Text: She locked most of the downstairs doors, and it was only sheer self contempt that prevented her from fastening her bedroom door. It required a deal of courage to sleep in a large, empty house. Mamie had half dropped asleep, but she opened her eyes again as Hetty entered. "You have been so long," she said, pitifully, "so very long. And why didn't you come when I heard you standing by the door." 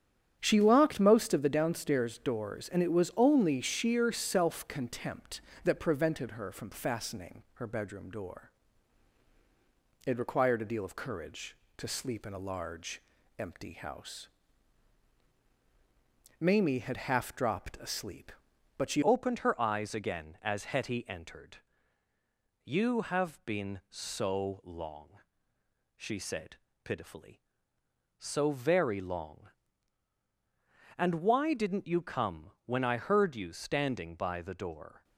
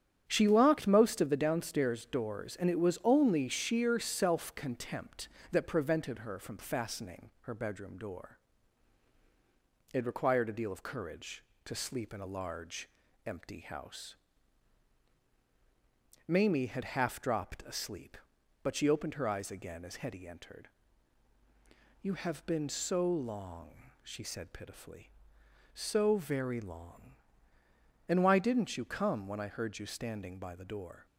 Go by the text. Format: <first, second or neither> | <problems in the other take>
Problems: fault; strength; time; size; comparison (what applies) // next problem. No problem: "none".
second | starts louder than the rest; strong; until 1.4 s; 9.5 dB; strong in the second // changes voice at "opened"; from 19.0 s on; 16.0 s long